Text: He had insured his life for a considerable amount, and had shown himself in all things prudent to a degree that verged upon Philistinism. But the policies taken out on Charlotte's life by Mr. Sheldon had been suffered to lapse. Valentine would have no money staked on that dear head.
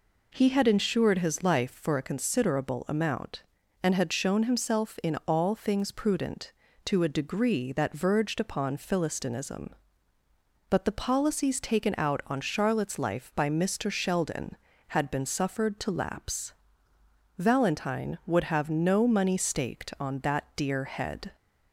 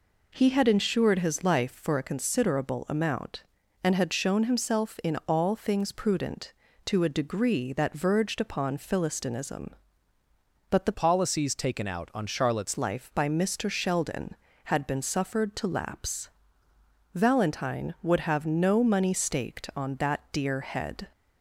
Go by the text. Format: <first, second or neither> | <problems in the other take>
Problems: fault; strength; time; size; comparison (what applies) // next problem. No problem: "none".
first | changes voice from "policies" to "Charlotte's"; from 10.9 to 12.7 s; 1.8 s long